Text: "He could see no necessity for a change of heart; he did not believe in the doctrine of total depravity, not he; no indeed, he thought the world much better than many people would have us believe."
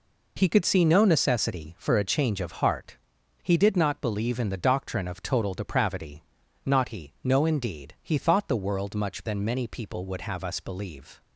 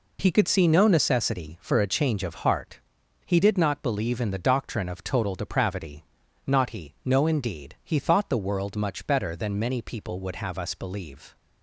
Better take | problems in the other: second | skips "better"; at 9.2 s

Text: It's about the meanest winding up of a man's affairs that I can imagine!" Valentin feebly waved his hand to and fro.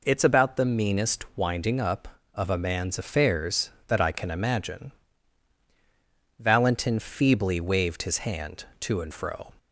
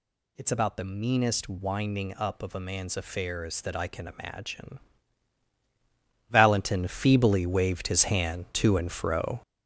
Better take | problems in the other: first | gets louder; throughout; 6.5 dB

